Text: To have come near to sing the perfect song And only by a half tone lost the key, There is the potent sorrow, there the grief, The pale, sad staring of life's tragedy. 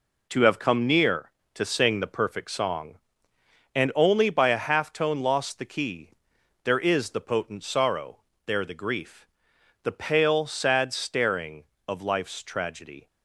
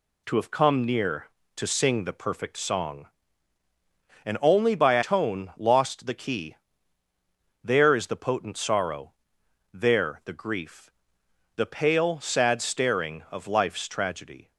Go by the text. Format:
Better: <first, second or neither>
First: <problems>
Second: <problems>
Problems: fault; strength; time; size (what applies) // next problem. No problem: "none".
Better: first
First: none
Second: skips "half"; at 5.0 s